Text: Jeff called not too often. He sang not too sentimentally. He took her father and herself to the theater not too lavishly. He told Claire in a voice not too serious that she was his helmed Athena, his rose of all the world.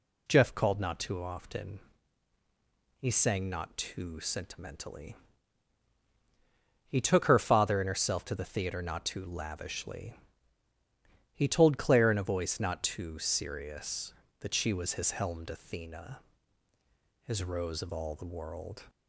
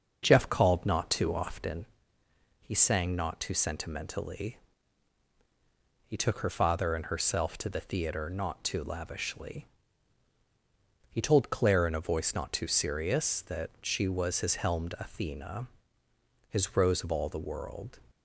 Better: first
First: none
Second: starts louder than the rest; until 1.8 s; 6.5 dB

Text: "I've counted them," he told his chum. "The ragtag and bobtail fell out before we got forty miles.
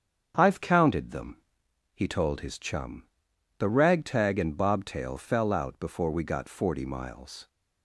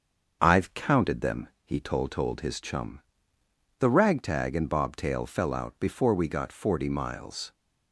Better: first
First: starts louder than the rest; strong; until 1.3 s; 7.5 dB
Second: starts louder than the rest; until 1.4 s; 7 dB // says "told" twice; at 2.1 s

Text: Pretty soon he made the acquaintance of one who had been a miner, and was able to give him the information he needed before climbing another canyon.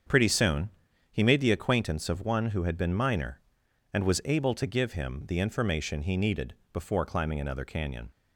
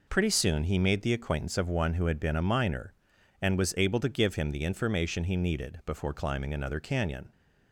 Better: second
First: starts louder than the rest; strong; until 1.5 s; 7.5 dB // pauses between "soon" and "he"; at 0.6 s; 0.42 s long // skips "a"; at 2.9 s // pauses between "needed" and "before"; slight; at 6.5 s; 0.18 s long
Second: none

